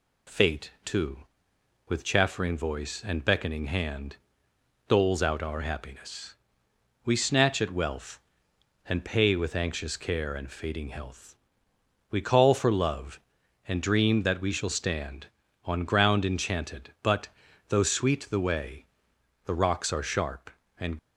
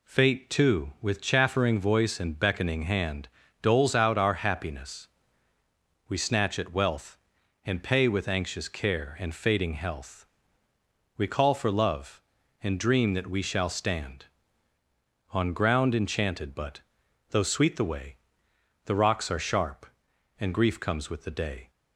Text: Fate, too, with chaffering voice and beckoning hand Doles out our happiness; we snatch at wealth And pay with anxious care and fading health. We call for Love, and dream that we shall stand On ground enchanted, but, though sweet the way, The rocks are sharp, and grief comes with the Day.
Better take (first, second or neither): second